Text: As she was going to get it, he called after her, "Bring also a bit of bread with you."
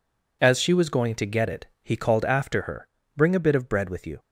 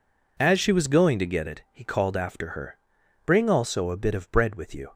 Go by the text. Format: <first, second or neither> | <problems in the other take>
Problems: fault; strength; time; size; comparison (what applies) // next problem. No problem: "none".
second | skips "also"; at 3.3 s